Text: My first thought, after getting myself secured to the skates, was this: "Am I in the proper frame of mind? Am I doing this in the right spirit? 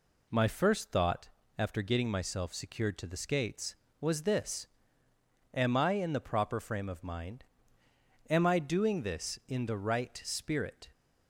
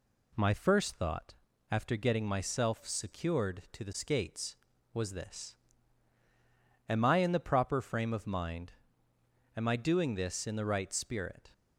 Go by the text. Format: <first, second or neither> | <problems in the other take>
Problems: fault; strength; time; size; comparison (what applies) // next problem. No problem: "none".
neither | none